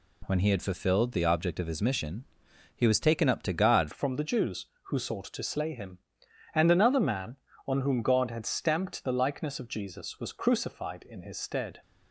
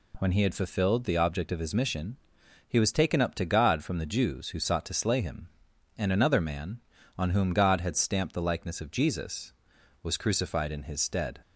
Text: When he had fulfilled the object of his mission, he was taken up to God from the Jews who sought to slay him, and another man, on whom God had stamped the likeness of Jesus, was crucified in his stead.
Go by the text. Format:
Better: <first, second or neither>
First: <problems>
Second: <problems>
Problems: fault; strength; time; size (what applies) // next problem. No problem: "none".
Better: second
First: changes voice at "from"; from 3.9 s on; 7.9 s long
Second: none